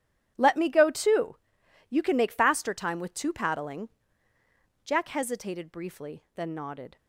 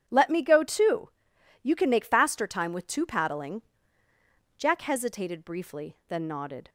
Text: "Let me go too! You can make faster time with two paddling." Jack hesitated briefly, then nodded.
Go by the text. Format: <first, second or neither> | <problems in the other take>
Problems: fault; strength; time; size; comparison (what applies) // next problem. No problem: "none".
second | gets quieter; strong; throughout; 14.5 dB // starts louder than the rest; strong; until 1.3 s; 10.5 dB; strong in the second